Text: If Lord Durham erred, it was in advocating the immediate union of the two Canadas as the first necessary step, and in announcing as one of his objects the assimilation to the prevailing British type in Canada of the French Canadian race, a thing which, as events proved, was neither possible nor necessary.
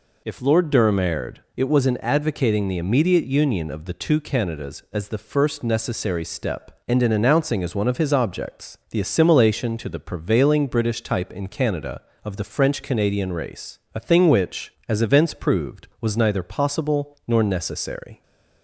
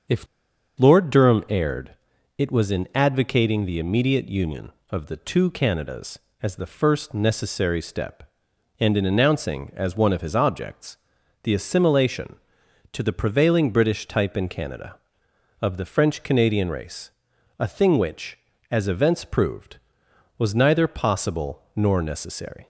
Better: first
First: none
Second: starts louder than the rest; until 1.6 s; 7 dB // pauses between "If" and "Lord"; noticeable; at 0.2 s; 0.52 s long // pauses between "objects" and "the"; noticeable; at 10.9 s; 0.46 s long

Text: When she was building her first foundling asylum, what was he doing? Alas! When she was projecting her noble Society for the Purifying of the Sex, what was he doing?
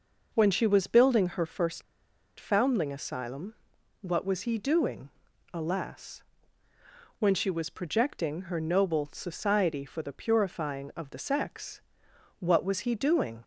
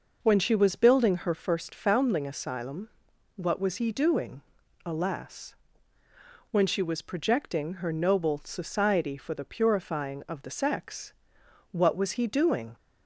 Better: second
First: pauses between "first" and "foundling"; noticeable; at 1.8 s; 0.56 s long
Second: none

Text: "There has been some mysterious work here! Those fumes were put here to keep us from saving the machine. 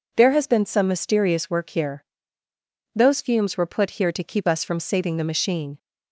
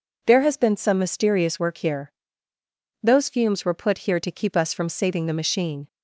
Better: neither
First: none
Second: none

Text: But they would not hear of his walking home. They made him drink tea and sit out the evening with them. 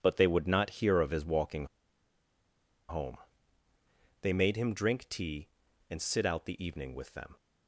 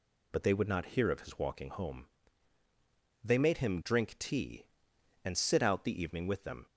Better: second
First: pauses between "walking" and "home"; at 1.6 s; 1.2 s long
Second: none

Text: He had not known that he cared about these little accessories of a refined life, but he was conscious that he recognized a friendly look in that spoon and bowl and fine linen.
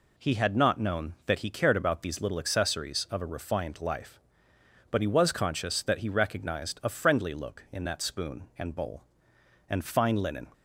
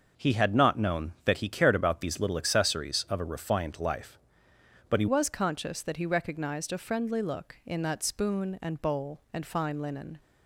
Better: first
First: none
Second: starts louder than the rest; until 1.3 s; 6.5 dB // changes voice at "was"; from 5.0 s on; 5.1 s long

